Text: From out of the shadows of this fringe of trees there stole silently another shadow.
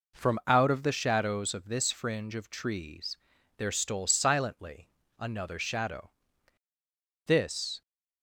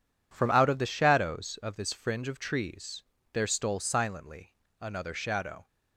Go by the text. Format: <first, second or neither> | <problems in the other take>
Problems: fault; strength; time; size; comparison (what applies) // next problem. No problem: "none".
second | pauses between "trees" and "there"; at 3.1 s; 0.40 s long; slight in the second // pauses between "silently" and "another"; slight; at 4.8 s; 0.32 s long; slight in the second // goes on to say "This"; from 7.2 s on; 0.56 s long